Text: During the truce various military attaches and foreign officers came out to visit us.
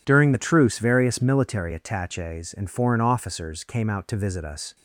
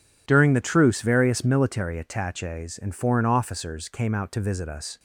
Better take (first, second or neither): neither